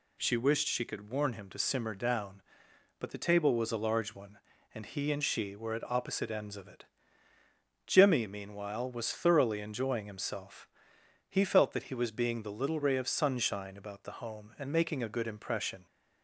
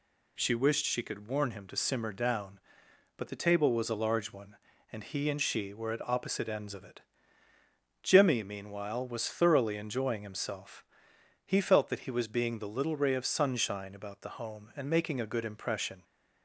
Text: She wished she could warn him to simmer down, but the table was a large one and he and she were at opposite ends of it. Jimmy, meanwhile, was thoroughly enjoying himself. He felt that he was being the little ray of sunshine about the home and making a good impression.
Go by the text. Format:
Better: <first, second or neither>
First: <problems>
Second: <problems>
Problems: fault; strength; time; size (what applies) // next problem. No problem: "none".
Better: neither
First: none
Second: none